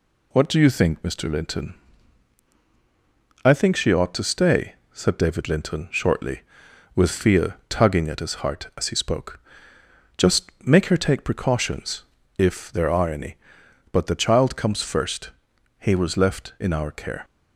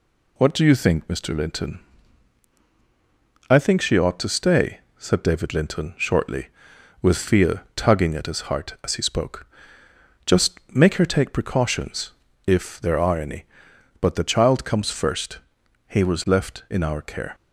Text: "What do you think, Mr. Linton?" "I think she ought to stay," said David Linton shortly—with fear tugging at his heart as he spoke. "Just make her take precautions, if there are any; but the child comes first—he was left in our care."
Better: neither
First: none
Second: none

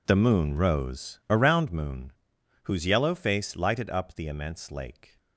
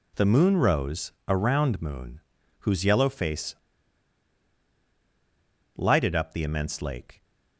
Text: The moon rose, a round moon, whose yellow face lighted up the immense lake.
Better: first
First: none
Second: pauses between "face" and "lighted"; strong; at 3.5 s; 2.1 s long

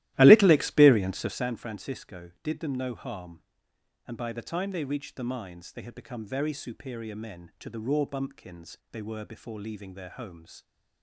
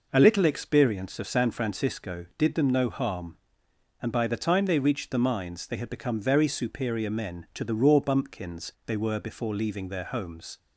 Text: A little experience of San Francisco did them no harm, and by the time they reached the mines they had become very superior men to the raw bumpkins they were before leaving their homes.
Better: second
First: starts louder than the rest; strong; until 1.5 s; 15.5 dB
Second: none

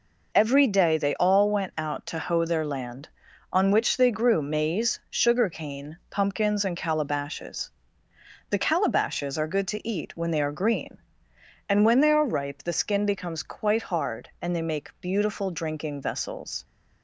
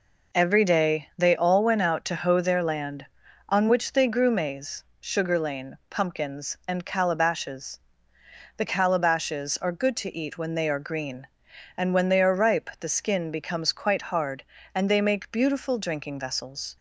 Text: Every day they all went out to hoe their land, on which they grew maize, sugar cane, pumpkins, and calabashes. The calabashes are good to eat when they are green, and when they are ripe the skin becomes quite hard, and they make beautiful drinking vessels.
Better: first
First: none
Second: says "lane" for "cane"; at 5.3 s

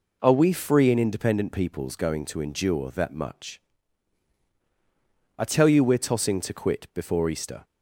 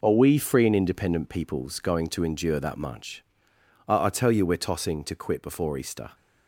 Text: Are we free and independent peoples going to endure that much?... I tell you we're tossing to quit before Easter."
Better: first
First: none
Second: says "I" twice; at 4.0 s

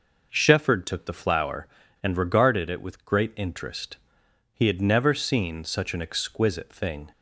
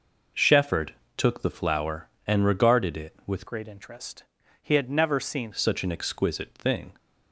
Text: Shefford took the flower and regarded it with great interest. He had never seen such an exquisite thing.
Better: first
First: none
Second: pauses between "Shefford" and "took"; slight; at 0.9 s; 0.22 s long // changes voice from "great" to "seen"; from 3.4 to 5.5 s; 2.1 s long

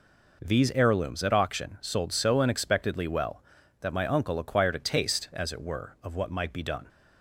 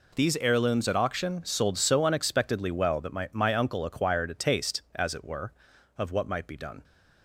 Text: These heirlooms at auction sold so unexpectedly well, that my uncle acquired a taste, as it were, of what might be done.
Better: first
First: none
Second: says "my" twice; at 3.3 s

